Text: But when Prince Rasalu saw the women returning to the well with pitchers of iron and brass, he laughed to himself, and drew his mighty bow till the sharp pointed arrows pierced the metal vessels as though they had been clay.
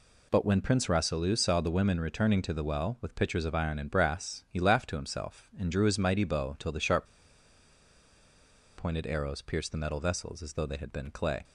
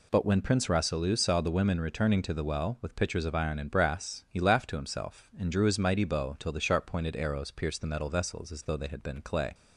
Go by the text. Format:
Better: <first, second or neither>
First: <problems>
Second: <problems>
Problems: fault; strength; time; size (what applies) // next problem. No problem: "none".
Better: second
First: pauses between "sharp" and "pointed"; strong; at 7.0 s; 1.7 s long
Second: none